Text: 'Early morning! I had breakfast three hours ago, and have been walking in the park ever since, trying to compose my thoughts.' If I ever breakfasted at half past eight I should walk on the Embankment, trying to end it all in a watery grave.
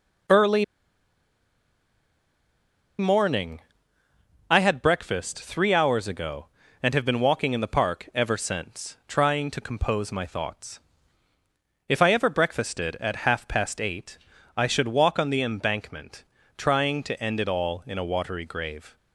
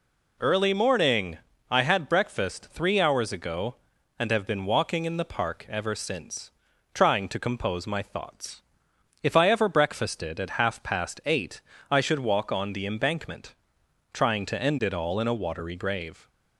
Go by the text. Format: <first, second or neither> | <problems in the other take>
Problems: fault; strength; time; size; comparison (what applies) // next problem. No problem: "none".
second | pauses between "Early" and "morning"; strong; at 0.6 s; 2.3 s long // pauses between "eight" and "I"; at 14.1 s; 0.38 s long; slight in the second